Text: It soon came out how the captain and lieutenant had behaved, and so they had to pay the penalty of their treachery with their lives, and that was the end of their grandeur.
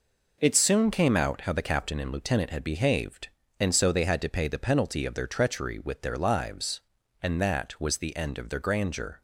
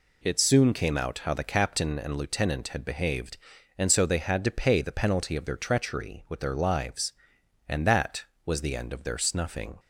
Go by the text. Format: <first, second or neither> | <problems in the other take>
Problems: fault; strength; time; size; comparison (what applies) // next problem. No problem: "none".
first | says "snuffing" for "grandeur"; at 9.1 s